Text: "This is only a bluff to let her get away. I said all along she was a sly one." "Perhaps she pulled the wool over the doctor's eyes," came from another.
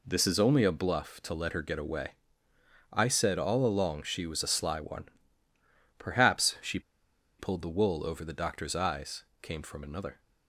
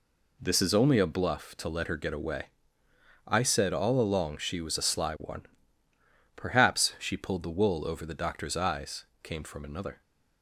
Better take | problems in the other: second | pauses between "she" and "pulled"; noticeable; at 6.7 s; 0.59 s long

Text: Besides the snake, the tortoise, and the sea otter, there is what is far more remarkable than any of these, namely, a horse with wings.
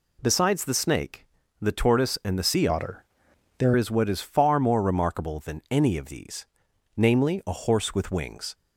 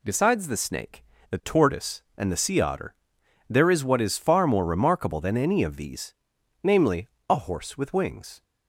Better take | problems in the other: second | changes voice from "otter" to "there"; from 2.6 to 3.7 s; 1.1 s long

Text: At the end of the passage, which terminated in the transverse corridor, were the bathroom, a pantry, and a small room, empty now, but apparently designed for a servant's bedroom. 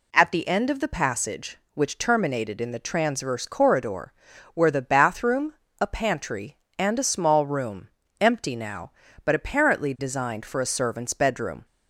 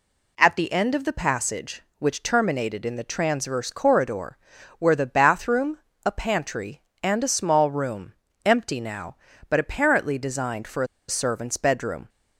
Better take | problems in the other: first | pauses between "a" and "servant's"; slight; at 10.8 s; 0.23 s long

